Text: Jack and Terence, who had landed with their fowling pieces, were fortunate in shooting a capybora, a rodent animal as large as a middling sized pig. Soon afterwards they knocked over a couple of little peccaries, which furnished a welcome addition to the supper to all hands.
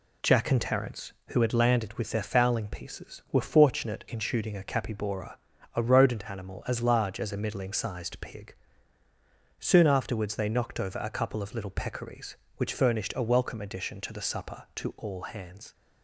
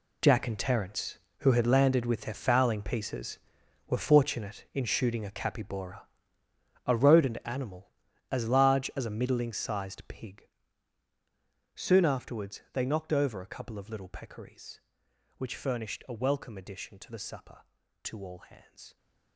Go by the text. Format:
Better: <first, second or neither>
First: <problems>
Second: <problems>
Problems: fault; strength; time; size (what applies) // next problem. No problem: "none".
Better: first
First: none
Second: gets quieter; strong; throughout; 13.5 dB